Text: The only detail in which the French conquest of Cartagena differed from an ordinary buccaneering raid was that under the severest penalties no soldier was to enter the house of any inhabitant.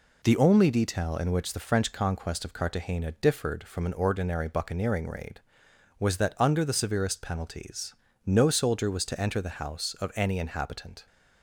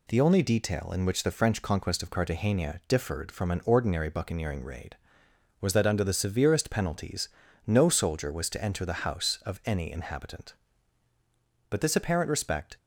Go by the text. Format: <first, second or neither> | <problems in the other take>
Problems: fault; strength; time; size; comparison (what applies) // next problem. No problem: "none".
first | pauses between "penalties" and "no"; at 7.2 s; 0.38 s long; slight in the first // goes on to say "But this apparent respect"; noticeable; from 11.6 s on; 1.0 s long